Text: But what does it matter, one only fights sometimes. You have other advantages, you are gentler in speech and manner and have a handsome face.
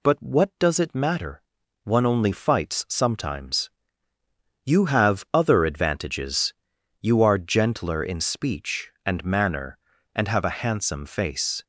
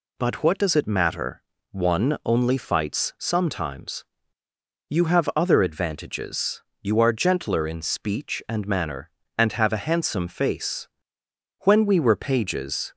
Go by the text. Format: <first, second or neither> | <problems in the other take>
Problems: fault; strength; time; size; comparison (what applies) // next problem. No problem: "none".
first | goes on to say "When we were pages"; noticeable; from 11.6 s on; 1.3 s long